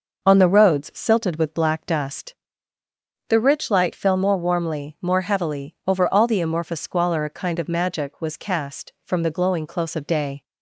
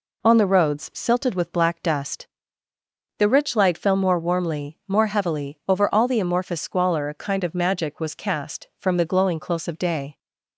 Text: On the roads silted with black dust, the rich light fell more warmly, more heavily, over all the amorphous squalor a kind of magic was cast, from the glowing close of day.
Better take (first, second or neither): neither